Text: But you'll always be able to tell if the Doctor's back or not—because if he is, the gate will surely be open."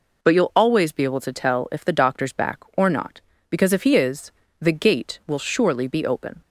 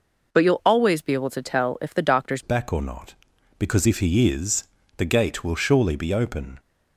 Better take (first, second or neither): first